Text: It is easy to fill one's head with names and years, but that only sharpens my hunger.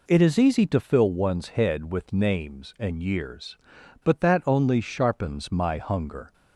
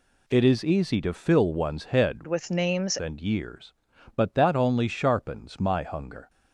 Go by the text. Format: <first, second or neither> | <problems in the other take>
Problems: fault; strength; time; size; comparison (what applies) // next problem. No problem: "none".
first | changes voice from "with" to "names"; from 2.2 to 2.9 s; 0.7 s long